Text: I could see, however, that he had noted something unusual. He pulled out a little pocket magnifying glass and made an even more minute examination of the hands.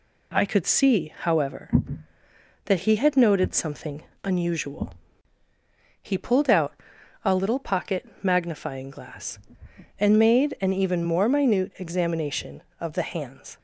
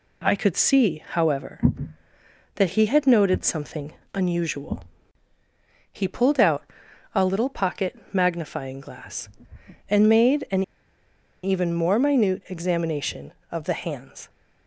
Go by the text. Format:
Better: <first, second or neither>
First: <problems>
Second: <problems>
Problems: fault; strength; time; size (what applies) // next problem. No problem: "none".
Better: first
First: pauses between "something" and "unusual"; slight; at 4.0 s; 0.22 s long // pauses between "out" and "a"; noticeable; at 6.7 s; 0.50 s long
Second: pauses between "something" and "unusual"; slight; at 3.9 s; 0.22 s long // pauses between "out" and "a"; noticeable; at 6.6 s; 0.50 s long // pauses between "an" and "even"; noticeable; at 10.6 s; 0.81 s long